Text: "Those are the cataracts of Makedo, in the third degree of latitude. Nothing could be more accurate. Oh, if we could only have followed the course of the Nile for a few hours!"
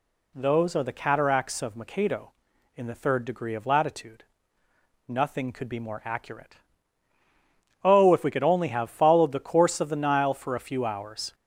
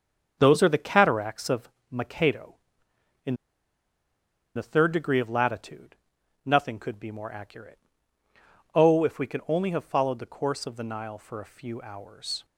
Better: first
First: none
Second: starts louder than the rest; strong; until 1.4 s; 7.5 dB // pauses between "of" and "Makedo"; slight; at 1.6 s; 0.22 s long // pauses between "in" and "the"; at 3.3 s; 1.2 s long

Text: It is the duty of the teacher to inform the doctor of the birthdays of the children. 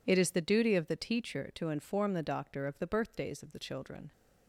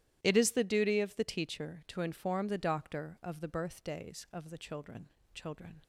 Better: first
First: none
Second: starts louder than the rest; strong; until 1.2 s; 13 dB // says "children" twice; at 5.3 s

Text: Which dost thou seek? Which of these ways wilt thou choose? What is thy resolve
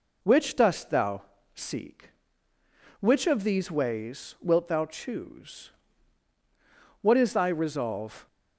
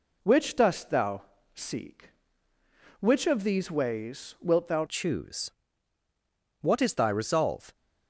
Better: first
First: pauses between "thou" and "seek"; slight; at 1.2 s; 0.32 s long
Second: pauses between "thou" and "seek"; slight; at 1.2 s; 0.32 s long // changes voice at "choose"; from 4.8 s on; 2.9 s long

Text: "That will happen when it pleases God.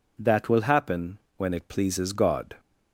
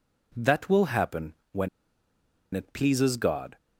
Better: first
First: pauses between "happen" and "when"; slight; at 1.1 s; 0.18 s long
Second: pauses between "happen" and "when"; slight; at 1.3 s; 0.16 s long // pauses between "when" and "it"; noticeable; at 1.6 s; 0.85 s long

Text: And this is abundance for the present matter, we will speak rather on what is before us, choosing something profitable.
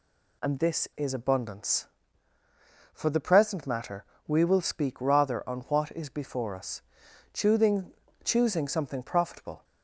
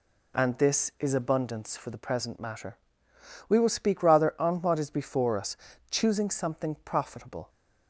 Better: second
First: says "choosing" twice; at 8.2 s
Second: none

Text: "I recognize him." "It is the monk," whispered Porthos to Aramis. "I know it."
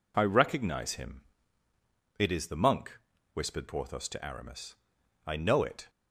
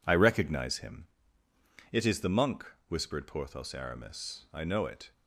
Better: first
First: none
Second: skips "to"; at 3.7 s

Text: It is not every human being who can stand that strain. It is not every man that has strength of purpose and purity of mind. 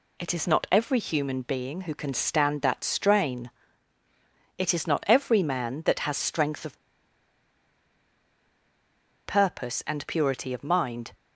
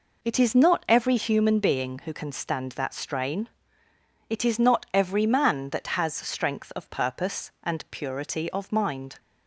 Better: second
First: pauses between "of" and "purpose"; strong; at 6.7 s; 2.4 s long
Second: none

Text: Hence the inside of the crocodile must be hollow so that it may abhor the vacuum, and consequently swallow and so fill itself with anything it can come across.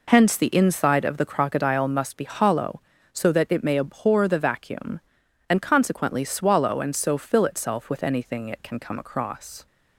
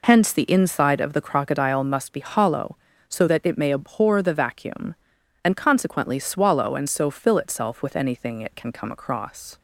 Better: neither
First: none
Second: none

